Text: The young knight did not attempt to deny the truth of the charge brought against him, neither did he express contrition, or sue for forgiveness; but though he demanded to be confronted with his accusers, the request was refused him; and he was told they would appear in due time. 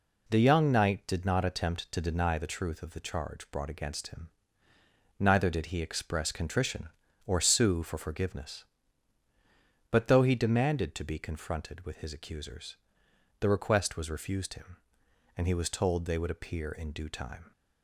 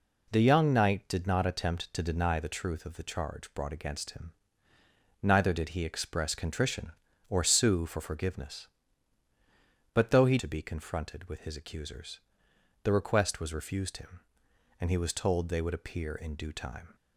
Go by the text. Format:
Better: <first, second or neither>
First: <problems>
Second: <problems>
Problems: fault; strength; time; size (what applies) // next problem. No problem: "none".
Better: first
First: none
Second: skips "demanded"; at 10.3 s